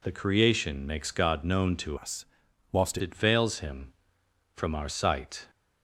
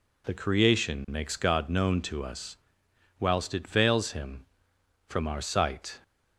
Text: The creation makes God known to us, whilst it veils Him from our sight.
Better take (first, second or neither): second